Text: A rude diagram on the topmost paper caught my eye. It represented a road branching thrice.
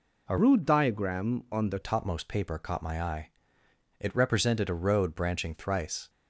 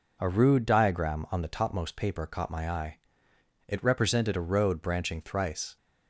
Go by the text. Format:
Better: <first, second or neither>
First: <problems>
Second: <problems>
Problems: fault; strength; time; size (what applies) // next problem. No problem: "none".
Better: second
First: changes voice from "rude" to "the"; from 0.3 to 1.8 s; 1.5 s long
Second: none